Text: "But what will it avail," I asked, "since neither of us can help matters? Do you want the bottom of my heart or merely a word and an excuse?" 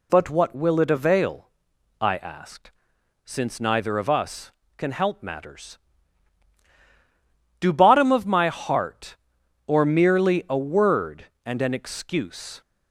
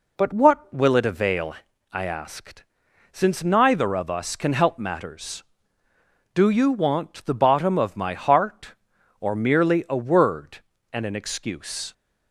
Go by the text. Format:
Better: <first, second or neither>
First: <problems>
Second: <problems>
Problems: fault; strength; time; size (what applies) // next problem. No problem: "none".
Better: second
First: skips "you want the"; at 7.7 s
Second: none